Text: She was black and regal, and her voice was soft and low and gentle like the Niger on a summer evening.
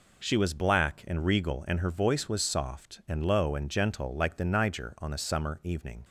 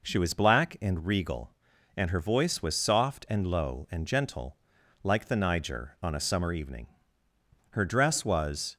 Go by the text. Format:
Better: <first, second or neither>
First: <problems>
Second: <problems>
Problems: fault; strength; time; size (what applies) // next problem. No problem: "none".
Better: first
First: none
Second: pauses between "gentle" and "like"; at 4.5 s; 0.44 s long // goes on to say "Her dress was"; noticeable; from 7.7 s on; 1.0 s long